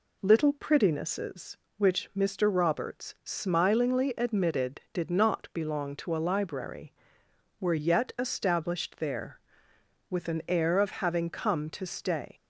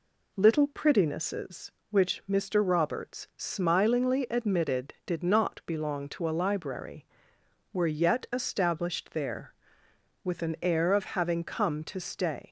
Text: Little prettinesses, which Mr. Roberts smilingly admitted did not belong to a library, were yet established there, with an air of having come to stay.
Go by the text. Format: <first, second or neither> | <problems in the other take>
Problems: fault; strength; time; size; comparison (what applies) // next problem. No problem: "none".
neither | none